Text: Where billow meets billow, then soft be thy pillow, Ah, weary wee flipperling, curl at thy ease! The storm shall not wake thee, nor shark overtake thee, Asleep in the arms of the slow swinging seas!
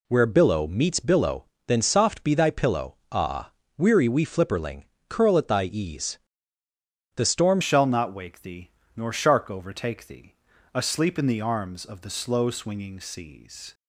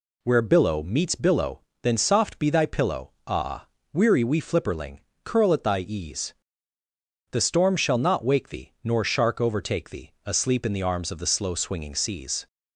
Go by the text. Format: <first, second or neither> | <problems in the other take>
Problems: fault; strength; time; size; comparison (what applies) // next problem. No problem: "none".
second | changes voice at "shall"; from 7.6 s on; 6.1 s long